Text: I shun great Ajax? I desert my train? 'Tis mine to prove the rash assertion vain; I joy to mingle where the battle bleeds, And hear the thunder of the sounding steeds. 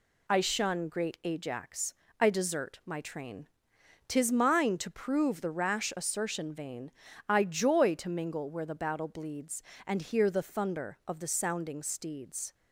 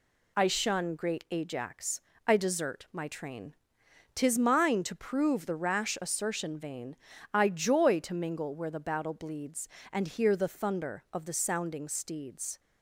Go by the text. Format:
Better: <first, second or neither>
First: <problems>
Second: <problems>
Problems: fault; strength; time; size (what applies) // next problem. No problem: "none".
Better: neither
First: none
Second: none